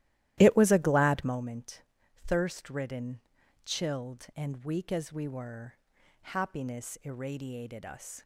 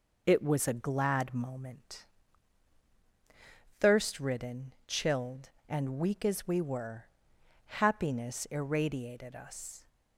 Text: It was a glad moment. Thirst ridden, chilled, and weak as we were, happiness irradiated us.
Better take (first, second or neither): second